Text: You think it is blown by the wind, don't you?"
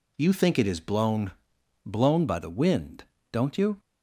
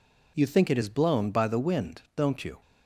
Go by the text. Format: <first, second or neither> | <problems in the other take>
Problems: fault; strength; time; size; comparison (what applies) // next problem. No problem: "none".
second | says "blown" twice; at 1.8 s